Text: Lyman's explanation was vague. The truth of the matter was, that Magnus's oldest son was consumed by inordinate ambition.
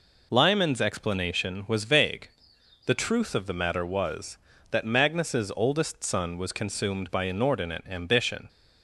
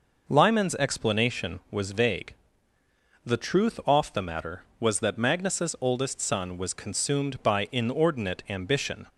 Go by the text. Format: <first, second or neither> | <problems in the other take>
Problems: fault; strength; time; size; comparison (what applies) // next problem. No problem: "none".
first | says "off" for "of"; at 3.8 s